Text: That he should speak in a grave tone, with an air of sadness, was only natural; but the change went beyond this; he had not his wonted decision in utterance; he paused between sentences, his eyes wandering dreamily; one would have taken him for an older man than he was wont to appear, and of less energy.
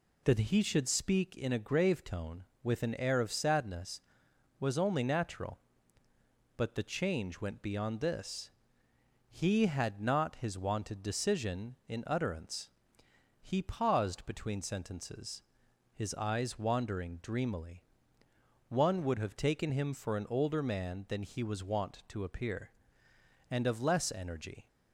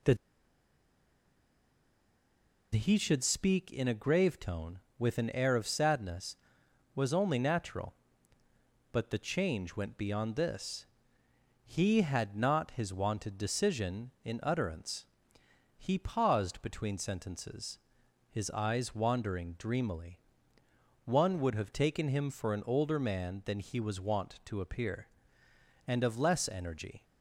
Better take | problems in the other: first | pauses between "That" and "he"; strong; at 0.1 s; 2.5 s long

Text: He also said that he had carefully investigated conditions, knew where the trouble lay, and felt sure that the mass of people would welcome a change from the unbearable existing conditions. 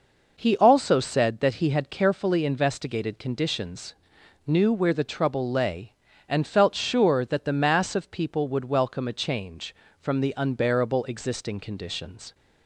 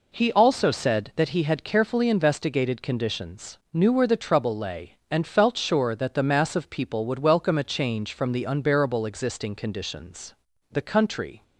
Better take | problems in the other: first | goes on to say "The country"; noticeable; from 10.7 s on; 0.72 s long

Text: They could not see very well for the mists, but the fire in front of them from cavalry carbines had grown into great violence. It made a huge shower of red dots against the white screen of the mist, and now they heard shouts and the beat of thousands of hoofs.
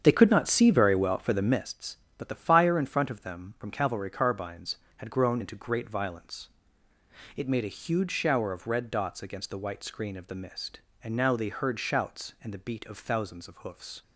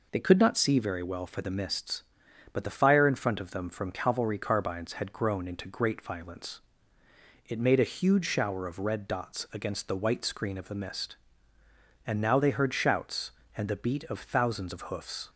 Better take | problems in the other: second | starts louder than the rest; strong; until 1.7 s; 8 dB

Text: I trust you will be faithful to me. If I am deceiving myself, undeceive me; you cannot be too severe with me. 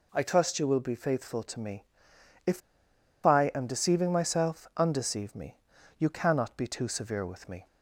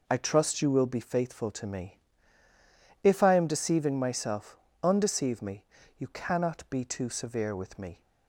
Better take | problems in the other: second | pauses between "If" and "I"; noticeable; at 2.6 s; 0.65 s long

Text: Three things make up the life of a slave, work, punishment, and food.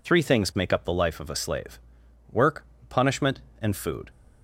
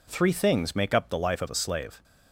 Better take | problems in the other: first | stops before "work punishment and food"; at 2.0 s

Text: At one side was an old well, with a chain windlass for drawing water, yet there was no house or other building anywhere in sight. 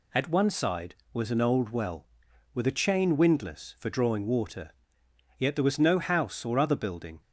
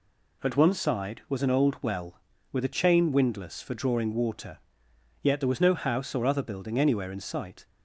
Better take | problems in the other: second | stops before "anywhere in sight"; at 7.2 s

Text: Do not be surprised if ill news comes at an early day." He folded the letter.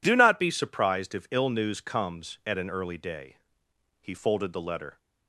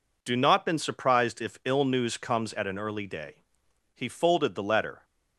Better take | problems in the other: first | says "been" for "be"; at 0.6 s

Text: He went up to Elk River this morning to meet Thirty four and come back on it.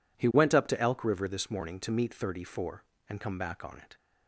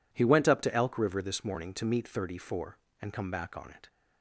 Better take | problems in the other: neither | none

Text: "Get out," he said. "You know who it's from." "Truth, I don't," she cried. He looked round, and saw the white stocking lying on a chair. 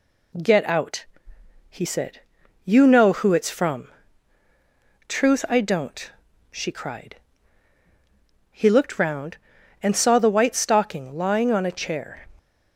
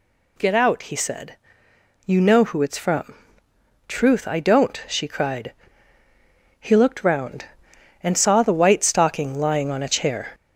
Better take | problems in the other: first | gets louder; throughout; 3.5 dB

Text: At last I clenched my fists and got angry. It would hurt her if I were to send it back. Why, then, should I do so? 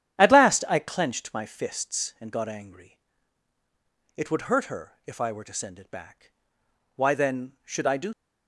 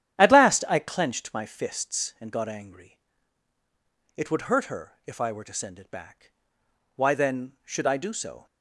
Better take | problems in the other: second | starts louder than the rest; strong; until 1.2 s; 9.5 dB; strong in the second // stops before "so"; at 8.1 s

